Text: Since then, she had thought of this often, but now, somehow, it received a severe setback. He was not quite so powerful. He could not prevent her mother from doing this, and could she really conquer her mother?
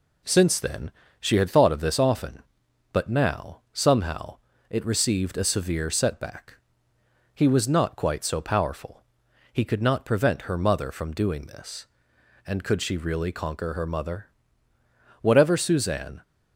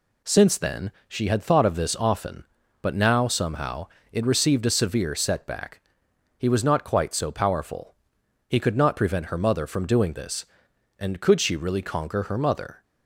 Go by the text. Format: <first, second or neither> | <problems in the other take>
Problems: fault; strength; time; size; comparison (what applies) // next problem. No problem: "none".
second | goes on to say "Whatever Suzanne"; noticeable; from 15.2 s on; 1.0 s long